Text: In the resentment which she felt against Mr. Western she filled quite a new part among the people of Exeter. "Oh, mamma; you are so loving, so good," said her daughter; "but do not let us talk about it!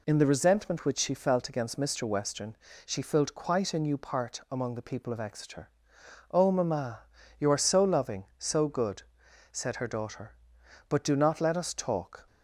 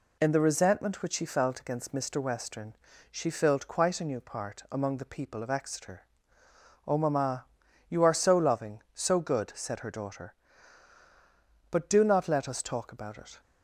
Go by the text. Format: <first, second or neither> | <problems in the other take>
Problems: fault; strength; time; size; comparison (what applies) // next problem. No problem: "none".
second | pauses between "Western" and "she"; slight; at 2.5 s; 0.30 s long; slight in the second // stops before "about it"; at 12.2 s